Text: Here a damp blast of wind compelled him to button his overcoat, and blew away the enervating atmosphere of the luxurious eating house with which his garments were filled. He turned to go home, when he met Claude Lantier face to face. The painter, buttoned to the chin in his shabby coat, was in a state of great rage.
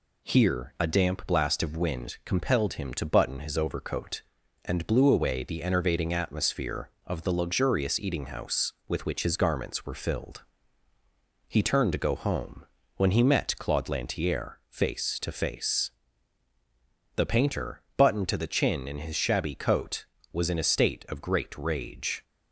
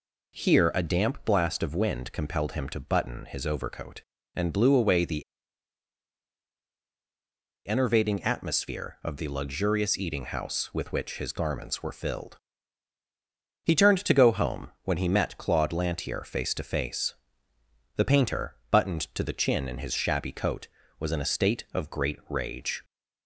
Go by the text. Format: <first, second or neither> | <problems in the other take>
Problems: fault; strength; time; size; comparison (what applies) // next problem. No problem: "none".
first | pauses between "the" and "enervating"; strong; at 5.2 s; 2.4 s long